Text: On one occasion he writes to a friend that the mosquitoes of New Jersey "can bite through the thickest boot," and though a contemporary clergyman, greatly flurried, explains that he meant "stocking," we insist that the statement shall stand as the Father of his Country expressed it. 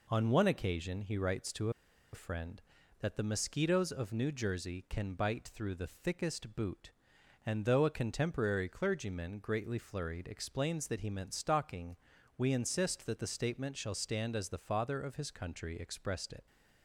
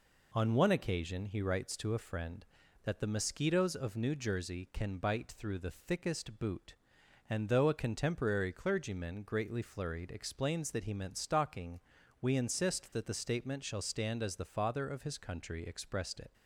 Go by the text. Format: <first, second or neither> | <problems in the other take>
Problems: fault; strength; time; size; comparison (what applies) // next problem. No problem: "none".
second | pauses between "to" and "a"; at 1.6 s; 0.43 s long